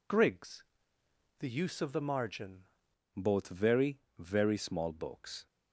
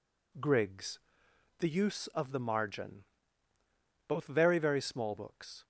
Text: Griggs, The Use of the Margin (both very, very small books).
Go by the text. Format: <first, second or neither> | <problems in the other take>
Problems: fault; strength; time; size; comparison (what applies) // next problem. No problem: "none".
second | changes voice at "both"; from 3.1 s on; 2.3 s long